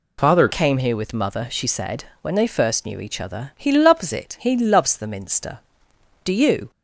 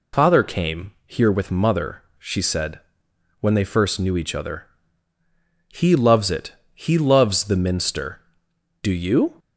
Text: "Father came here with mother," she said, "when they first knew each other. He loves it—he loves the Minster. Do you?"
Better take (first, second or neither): second